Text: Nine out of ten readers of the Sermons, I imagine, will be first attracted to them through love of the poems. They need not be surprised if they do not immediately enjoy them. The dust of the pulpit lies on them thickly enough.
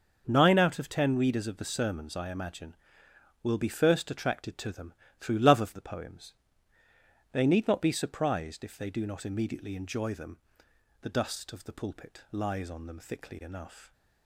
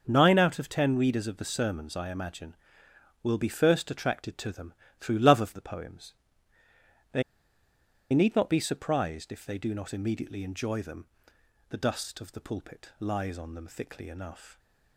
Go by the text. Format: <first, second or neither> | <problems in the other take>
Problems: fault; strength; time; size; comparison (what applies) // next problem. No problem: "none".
first | starts louder than the rest; noticeable; until 1.0 s; 6 dB; noticeable in the first // pauses between "them" and "through"; slight; at 4.7 s; 0.26 s long; slight in the first // pauses between "They" and "need"; noticeable; at 7.2 s; 0.89 s long